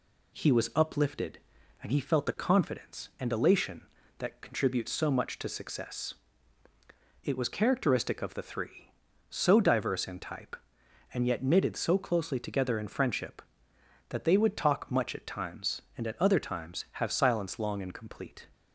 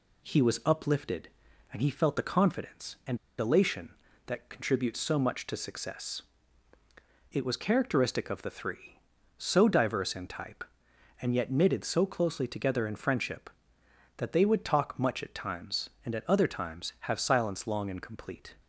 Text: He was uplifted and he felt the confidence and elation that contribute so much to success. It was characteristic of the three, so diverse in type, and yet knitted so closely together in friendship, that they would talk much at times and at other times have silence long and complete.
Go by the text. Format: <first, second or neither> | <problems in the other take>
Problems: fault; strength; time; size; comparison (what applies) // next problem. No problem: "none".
first | pauses between "and" and "elation"; slight; at 3.1 s; 0.23 s long